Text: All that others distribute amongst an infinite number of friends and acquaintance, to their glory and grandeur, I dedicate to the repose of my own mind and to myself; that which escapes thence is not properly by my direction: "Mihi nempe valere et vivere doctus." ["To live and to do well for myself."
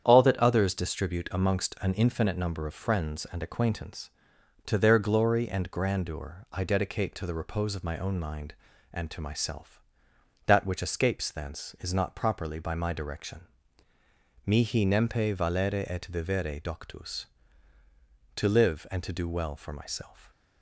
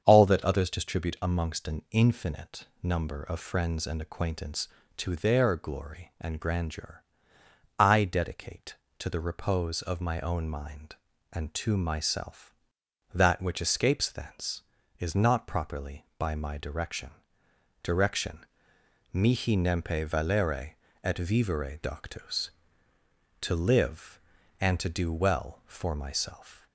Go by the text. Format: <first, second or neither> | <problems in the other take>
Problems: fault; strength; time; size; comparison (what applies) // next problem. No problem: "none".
first | starts louder than the rest; strong; until 1.0 s; 7.5 dB; strong in the first // pauses between "infinite" and "number"; slight; at 2.6 s; 0.16 s long // says "direction" twice; at 17.8 s // pauses between "valere" and "et"; slight; at 20.7 s; 0.30 s long